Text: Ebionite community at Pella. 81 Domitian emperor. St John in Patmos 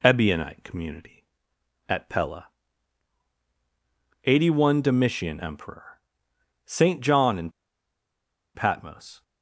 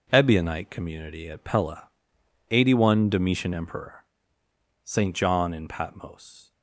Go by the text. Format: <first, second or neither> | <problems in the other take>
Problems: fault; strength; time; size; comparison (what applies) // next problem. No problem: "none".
second | pauses between "in" and "Patmos"; at 7.4 s; 1.0 s long